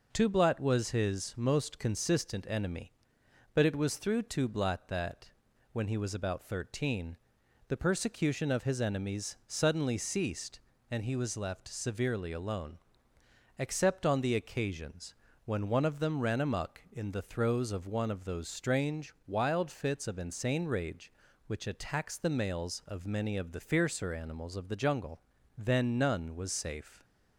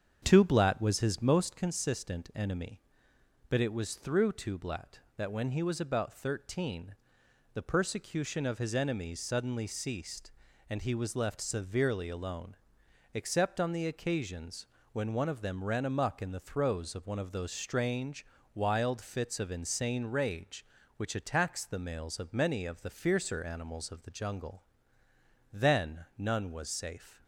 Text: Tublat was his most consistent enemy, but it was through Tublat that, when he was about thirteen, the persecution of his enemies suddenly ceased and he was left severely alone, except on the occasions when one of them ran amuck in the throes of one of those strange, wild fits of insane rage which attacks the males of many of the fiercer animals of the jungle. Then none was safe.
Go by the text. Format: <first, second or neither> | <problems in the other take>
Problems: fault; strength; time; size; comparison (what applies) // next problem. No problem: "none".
first | starts louder than the rest; strong; until 1.6 s; 7.5 dB // pauses between "occasions" and "when"; slight; at 14.6 s; 0.26 s long; slight in the first